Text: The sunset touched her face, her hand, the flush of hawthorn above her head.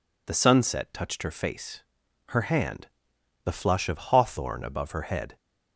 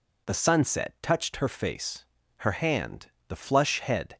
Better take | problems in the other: first | skips "of hawthorn above her"; at 3.8 s

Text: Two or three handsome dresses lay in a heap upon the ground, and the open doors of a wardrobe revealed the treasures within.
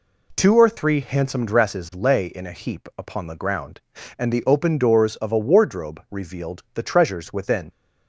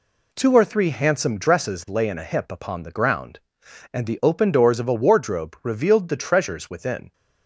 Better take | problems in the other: first | says "hip" for "heap"; at 2.2 s

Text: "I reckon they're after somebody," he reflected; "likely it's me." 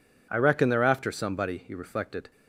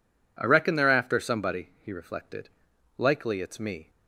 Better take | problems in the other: second | stops before "likely it's me"; at 2.3 s

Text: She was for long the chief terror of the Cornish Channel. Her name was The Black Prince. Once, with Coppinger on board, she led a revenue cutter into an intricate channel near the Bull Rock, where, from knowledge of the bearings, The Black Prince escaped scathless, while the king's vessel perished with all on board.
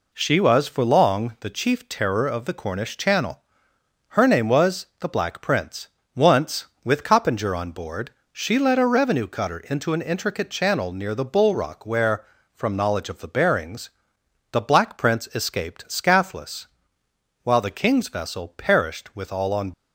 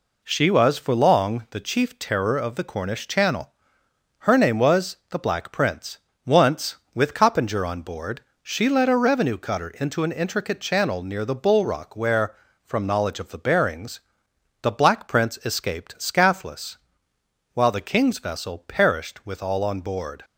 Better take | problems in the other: second | stops before "board"; at 19.7 s

